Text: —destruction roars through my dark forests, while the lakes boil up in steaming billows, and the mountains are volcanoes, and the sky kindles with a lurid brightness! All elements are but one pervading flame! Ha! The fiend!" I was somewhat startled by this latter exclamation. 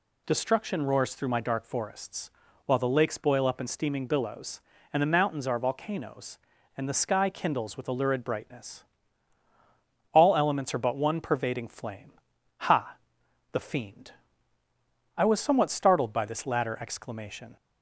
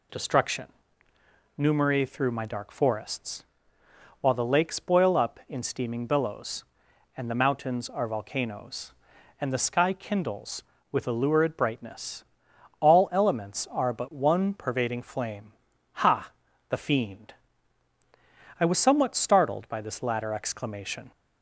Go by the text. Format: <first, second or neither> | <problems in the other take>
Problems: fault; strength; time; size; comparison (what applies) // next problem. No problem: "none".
first | says "numeri" for "roars"; at 1.5 s